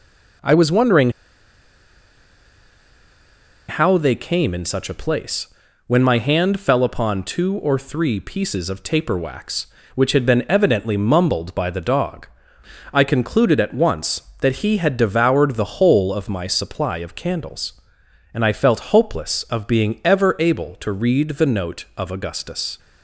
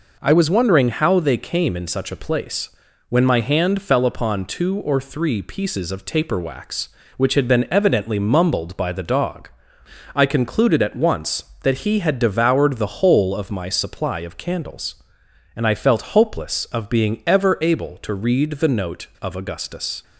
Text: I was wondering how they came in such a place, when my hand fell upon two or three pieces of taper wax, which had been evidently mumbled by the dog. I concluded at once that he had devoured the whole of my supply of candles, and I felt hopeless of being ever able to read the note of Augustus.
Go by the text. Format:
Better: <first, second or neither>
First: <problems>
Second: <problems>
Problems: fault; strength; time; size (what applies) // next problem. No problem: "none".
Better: second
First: pauses between "wondering" and "how"; strong; at 1.0 s; 2.5 s long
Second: none